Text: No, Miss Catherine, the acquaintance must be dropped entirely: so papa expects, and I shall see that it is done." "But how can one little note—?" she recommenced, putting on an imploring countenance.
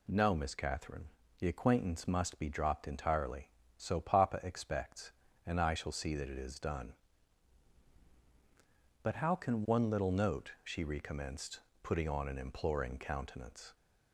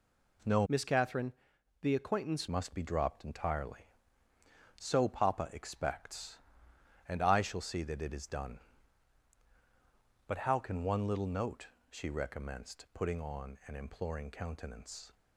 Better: first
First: none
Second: changes voice from "Miss" to "acquaintance"; from 0.6 to 2.4 s; 1.8 s long

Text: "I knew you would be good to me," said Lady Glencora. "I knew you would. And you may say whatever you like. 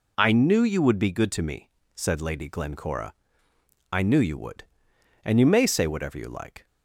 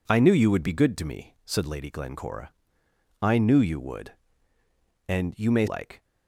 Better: first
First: none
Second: skips "say whatever you"; at 5.6 s

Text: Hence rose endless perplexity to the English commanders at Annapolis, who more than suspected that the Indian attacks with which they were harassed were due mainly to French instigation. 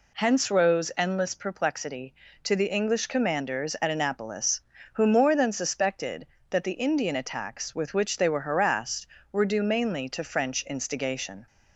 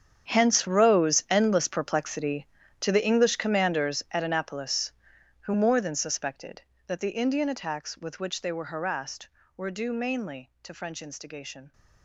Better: first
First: none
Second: gets quieter; strong; throughout; 17 dB

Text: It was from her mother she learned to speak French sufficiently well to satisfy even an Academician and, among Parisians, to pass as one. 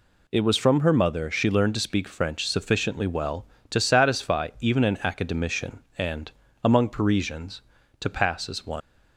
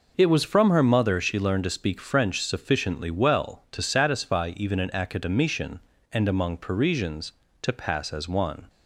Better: second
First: leaves "one" unfinished; at 8.8 s; 105 ms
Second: none

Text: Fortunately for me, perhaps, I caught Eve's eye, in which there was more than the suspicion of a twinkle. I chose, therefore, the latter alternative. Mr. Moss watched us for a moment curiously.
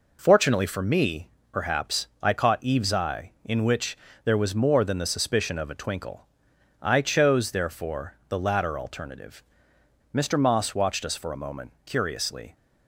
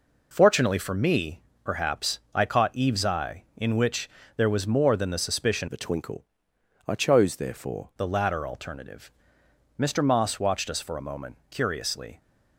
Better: first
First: pauses between "which" and "there"; slight; at 3.9 s; 0.30 s long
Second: pauses between "which" and "there"; slight; at 4.0 s; 0.30 s long // changes voice from "of" to "therefore"; from 5.6 to 7.9 s; 2.3 s long

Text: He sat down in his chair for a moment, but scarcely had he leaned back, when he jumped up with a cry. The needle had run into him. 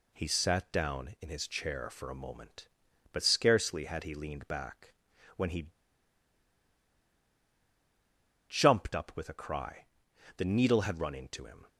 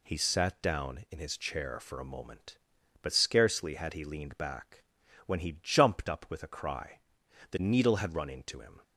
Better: second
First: pauses between "he" and "jumped"; strong; at 5.6 s; 2.7 s long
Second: none

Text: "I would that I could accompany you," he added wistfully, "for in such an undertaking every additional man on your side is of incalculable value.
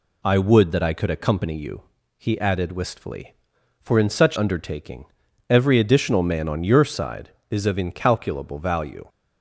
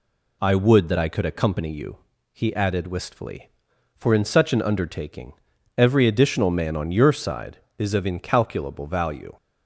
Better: second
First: skips "an"; at 4.3 s // pauses between "undertaking" and "every"; at 5.0 s; 0.42 s long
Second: pauses between "undertaking" and "every"; at 5.3 s; 0.42 s long

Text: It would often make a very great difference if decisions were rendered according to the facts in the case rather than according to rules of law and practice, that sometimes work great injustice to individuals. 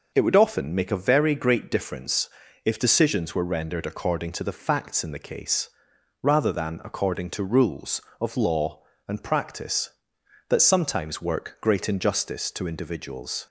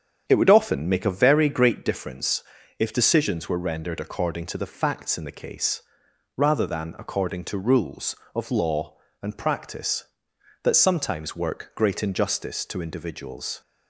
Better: first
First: pauses between "difference" and "if"; slight; at 2.2 s; 0.36 s long // pauses between "case" and "rather"; noticeable; at 5.7 s; 0.52 s long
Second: starts louder than the rest; strong; until 1.8 s; 8 dB // pauses between "difference" and "if"; slight; at 2.4 s; 0.36 s long // pauses between "case" and "rather"; noticeable; at 5.8 s; 0.54 s long

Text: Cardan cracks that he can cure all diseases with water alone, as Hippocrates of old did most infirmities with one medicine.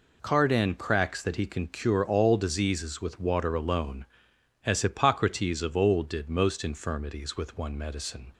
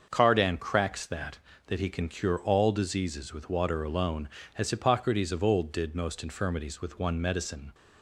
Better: first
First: none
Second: starts louder than the rest; until 1.1 s; 6.5 dB // says "that" twice; at 1.6 s

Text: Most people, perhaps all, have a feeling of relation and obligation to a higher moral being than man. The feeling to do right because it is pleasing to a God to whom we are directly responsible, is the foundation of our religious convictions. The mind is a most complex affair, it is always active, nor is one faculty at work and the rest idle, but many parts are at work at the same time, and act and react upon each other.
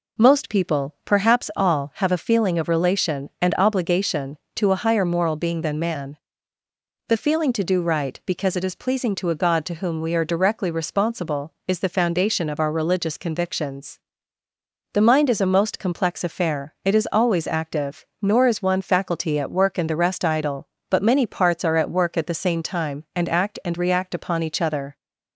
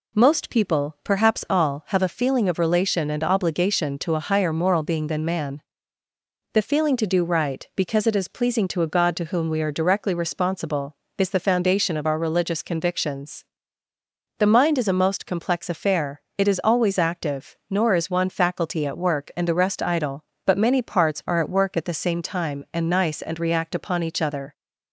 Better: first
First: none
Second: says "nice" for "act"; at 22.8 s

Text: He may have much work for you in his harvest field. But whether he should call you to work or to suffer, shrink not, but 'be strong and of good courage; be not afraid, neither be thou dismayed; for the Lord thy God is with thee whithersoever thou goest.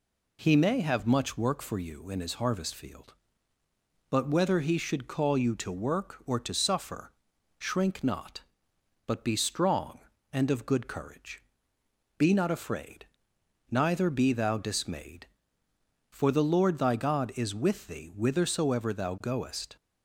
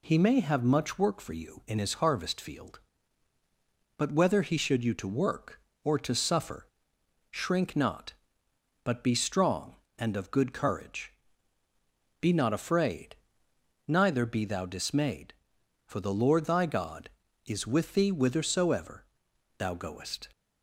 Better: first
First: none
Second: skips "call"; at 4.8 s // pauses between "whithersoever" and "thou"; noticeable; at 19.0 s; 0.52 s long

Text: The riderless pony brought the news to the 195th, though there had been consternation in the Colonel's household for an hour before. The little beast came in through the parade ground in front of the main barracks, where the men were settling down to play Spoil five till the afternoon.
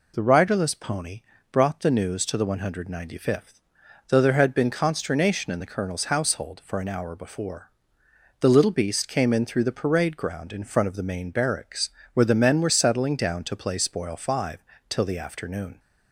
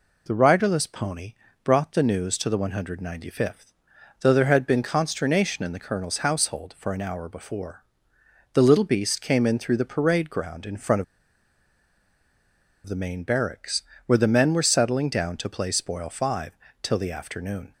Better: first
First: pauses between "pony" and "brought"; slight; at 1.2 s; 0.28 s long // pauses between "five" and "till"; slight; at 14.5 s; 0.28 s long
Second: pauses between "pony" and "brought"; slight; at 1.3 s; 0.28 s long // pauses between "of" and "the"; strong; at 11.0 s; 1.8 s long // pauses between "five" and "till"; slight; at 16.5 s; 0.28 s long

